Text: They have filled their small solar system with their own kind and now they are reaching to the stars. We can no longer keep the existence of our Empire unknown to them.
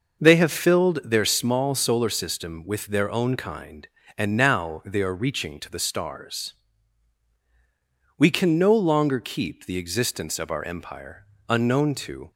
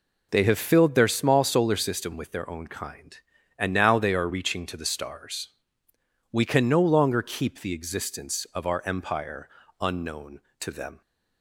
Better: second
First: pauses between "Empire" and "unknown"; slight; at 11.2 s; 0.22 s long // stops before "them"; at 12.3 s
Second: pauses between "Empire" and "unknown"; slight; at 9.4 s; 0.32 s long

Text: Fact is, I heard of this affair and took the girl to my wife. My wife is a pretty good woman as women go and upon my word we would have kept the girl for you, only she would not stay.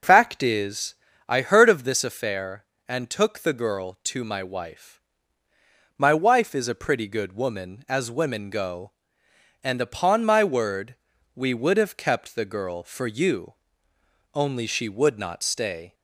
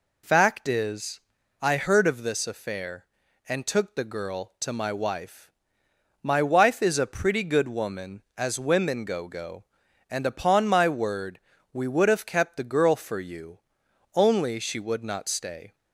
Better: first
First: pauses between "word" and "we"; at 10.9 s; 0.38 s long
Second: says "go" twice; at 9.2 s // pauses between "word" and "we"; slight; at 11.4 s; 0.34 s long

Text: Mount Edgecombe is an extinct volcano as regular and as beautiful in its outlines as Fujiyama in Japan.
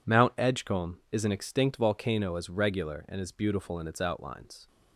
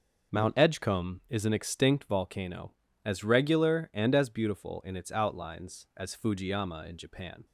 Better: second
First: stops before "as Fujiyama in Japan"; at 4.6 s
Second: none

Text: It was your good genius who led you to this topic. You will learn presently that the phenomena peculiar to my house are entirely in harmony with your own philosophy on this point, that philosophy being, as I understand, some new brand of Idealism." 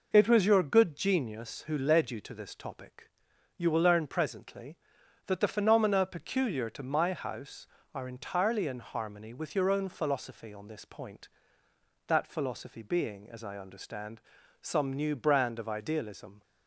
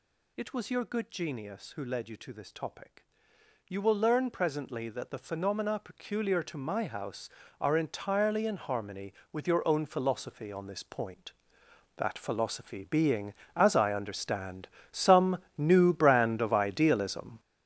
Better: first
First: none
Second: gets louder; strong; throughout; 9 dB // pauses between "some" and "new"; slight; at 15.3 s; 0.20 s long

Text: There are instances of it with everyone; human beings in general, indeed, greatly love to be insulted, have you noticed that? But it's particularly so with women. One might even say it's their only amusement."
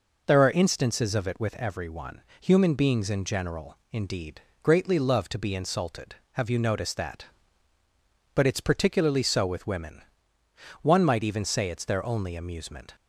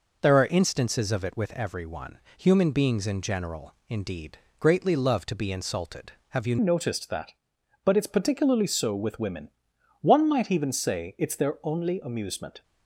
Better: first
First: none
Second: changes voice at "noticed"; from 6.5 s on; 6.1 s long

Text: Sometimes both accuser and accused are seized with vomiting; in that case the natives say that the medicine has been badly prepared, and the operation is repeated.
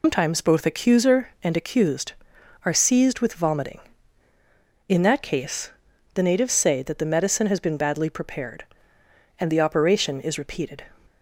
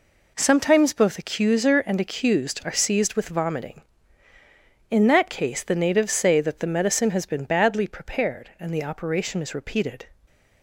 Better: second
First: loses the start of "Sometimes"; at 0.0 s; 165 ms // pauses between "case" and "the"; at 5.7 s; 0.42 s long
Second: none

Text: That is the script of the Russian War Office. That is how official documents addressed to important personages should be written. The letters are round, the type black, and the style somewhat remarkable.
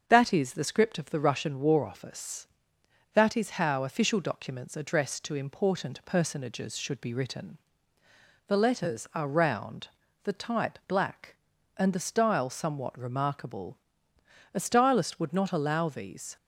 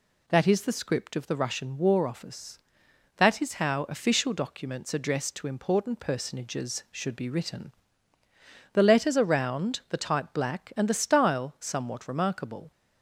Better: second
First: starts louder than the rest; until 1.0 s; 7 dB // goes on to say "A stylist would not allow these"; strong; from 14.5 s on; 1.8 s long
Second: none

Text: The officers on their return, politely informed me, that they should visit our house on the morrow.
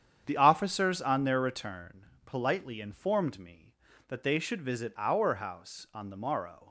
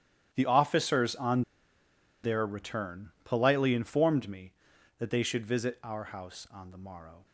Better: first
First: starts louder than the rest; strong; until 1.2 s; 8.5 dB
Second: starts louder than the rest; strong; until 1.3 s; 10.5 dB // pauses between "on" and "their"; noticeable; at 1.4 s; 0.81 s long

